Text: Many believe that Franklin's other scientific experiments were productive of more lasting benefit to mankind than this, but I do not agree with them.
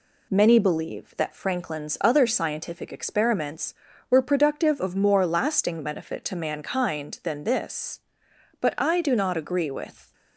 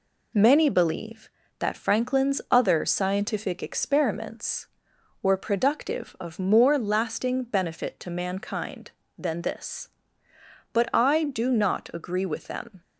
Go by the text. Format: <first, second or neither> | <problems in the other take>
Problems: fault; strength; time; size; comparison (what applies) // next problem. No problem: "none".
second | stops before "them"; at 10.1 s